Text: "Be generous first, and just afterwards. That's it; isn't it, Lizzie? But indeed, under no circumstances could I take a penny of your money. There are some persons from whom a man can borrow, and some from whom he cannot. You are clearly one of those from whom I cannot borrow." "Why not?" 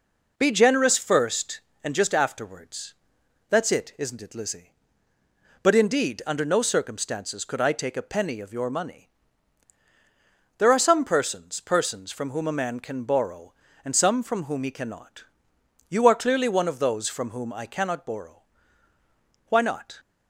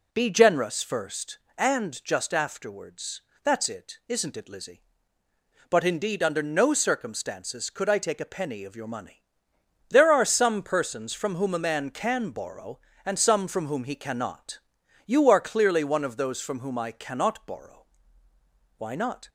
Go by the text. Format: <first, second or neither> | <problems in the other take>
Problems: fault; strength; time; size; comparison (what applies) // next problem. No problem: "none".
second | says "persons" twice; at 11.6 s